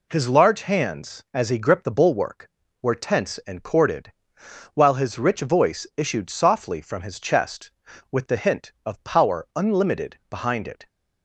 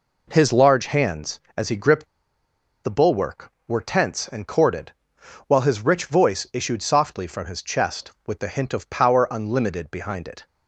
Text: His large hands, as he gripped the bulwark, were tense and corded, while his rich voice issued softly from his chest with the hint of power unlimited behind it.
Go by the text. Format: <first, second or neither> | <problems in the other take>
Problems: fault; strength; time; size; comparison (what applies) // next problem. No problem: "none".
first | pauses between "gripped" and "the"; noticeable; at 2.0 s; 0.79 s long